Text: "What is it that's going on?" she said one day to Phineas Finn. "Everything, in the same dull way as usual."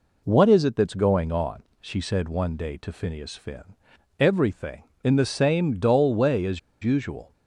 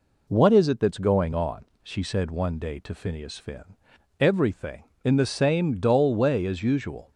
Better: second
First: pauses between "as" and "usual"; slight; at 6.5 s; 0.24 s long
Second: none

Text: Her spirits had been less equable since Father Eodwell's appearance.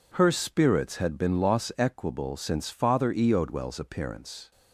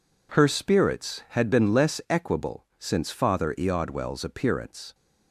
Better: second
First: says "loss" for "less"; at 1.4 s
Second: none

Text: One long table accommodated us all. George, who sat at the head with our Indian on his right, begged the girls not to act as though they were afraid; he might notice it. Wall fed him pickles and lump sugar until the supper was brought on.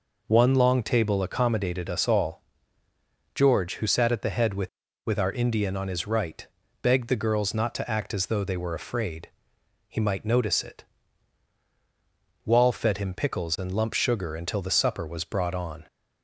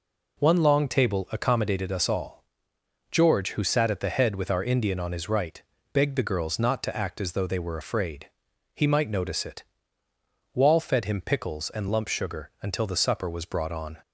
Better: second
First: says "with" twice; at 5.0 s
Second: none

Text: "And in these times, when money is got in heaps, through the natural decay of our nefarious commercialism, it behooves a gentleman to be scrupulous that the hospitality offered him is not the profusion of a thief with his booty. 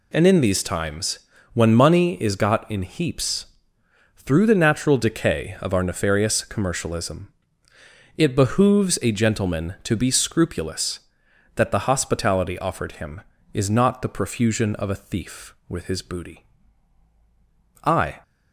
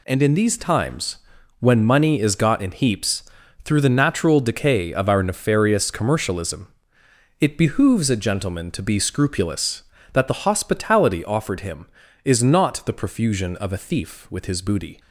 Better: second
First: goes on to say "I"; slight; from 17.8 s on; 0.38 s long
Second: none

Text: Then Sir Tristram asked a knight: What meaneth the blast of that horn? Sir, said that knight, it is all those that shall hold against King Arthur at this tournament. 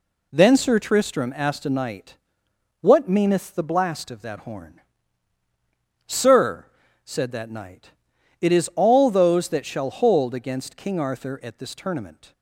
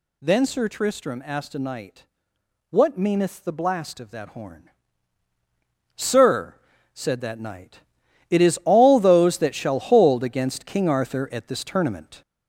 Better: first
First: none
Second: gets louder; noticeable; throughout; 4.5 dB

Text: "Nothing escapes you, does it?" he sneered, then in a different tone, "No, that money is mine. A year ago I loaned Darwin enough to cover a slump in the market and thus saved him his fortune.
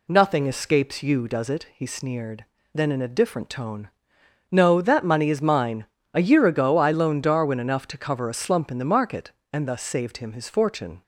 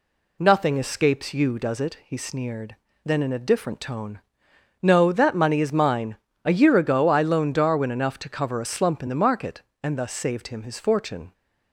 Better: neither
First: none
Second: none

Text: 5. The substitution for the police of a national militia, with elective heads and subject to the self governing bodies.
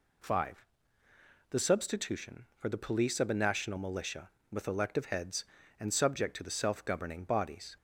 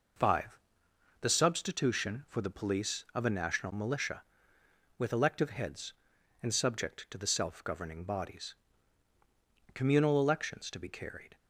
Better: first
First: none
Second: goes on to say "Communal elections to be carried"; from 9.7 s on; 1.6 s long

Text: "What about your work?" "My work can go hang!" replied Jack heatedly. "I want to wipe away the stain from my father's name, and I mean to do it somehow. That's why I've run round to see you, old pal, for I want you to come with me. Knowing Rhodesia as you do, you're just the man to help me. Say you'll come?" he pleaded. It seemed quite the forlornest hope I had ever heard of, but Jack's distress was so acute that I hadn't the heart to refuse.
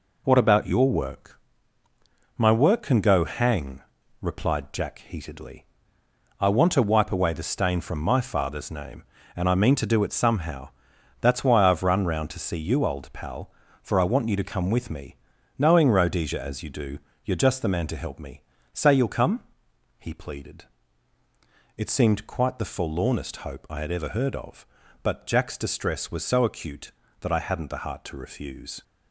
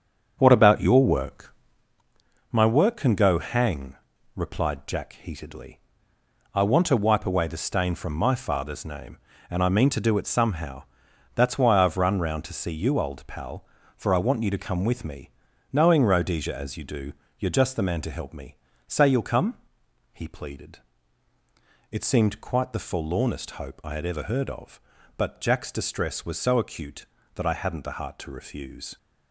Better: first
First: none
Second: starts louder than the rest; strong; until 2.0 s; 7.5 dB

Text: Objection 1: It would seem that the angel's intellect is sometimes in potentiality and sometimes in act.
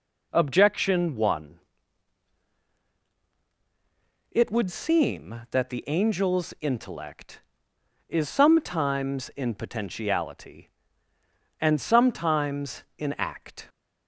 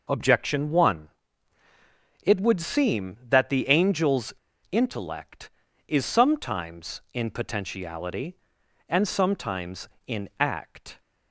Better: first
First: none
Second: pauses between "angel's" and "intellect"; at 4.3 s; 0.37 s long

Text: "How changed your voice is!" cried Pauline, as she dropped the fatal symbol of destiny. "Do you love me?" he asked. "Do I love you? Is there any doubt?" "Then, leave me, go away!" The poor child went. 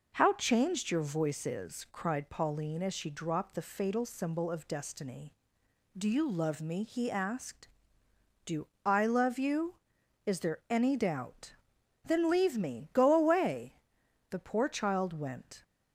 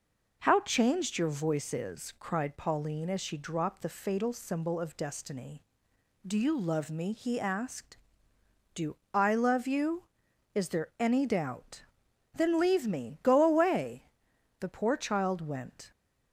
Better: neither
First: pauses between "Do" and "I"; slight; at 8.6 s; 0.18 s long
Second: pauses between "Do" and "I"; slight; at 8.9 s; 0.17 s long

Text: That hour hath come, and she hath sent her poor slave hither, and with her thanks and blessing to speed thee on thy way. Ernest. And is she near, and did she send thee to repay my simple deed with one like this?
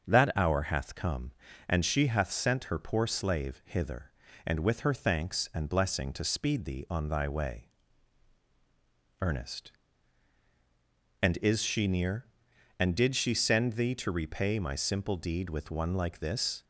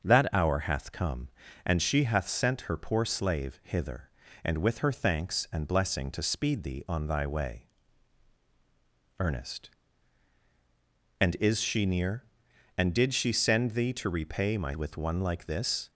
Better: first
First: starts louder than the rest; until 1.0 s; 6.5 dB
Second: starts louder than the rest; until 1.0 s; 6.5 dB // skips "simple deed"; at 14.7 s

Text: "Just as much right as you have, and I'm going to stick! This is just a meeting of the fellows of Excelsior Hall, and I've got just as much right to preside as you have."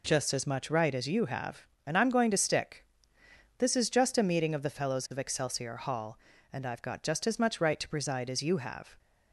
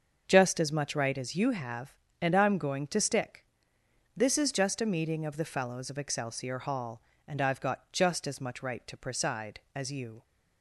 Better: first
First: none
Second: starts louder than the rest; until 1.2 s; 6.5 dB // stops before "have"; at 10.2 s

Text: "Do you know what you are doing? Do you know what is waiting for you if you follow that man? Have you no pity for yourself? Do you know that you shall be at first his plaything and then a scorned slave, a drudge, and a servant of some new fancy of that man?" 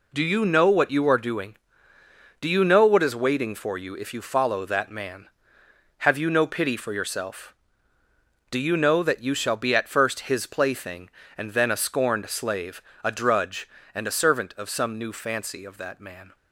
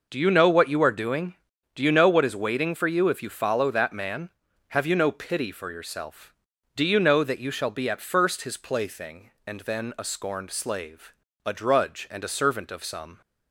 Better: first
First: none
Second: stops before "new fancy of that man"; at 13.2 s

